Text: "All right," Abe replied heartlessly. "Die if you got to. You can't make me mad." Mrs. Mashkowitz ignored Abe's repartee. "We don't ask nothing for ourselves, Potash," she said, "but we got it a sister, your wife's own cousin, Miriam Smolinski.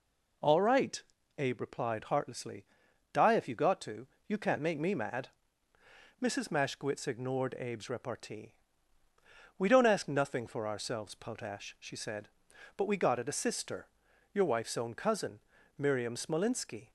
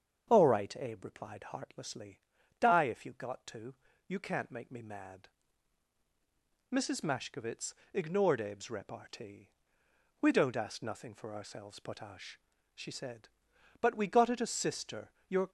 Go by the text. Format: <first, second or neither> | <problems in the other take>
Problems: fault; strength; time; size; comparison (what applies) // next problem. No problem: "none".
first | starts louder than the rest; strong; until 1.3 s; 7.5 dB // pauses between "Mashkowitz" and "ignored"; slight; at 7.7 s; 0.20 s long // stops before "wife's own cousin Miriam Smolinski"; at 15.4 s